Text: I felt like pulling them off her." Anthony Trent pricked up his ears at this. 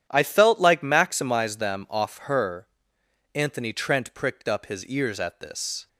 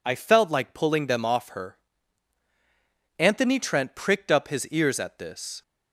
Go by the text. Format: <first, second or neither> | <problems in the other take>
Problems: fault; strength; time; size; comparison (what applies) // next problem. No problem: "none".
second | starts louder than the rest; strong; until 1.1 s; 10 dB // says "maximize" for "pulling"; at 0.7 s